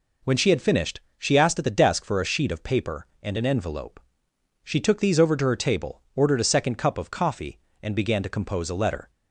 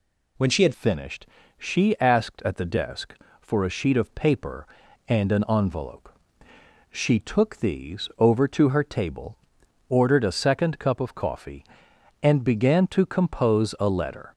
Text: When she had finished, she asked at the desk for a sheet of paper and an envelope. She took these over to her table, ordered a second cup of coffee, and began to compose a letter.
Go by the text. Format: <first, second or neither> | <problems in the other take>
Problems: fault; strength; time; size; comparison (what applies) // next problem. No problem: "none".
first | changes voice at "finished"; from 0.7 s on; 13.6 s long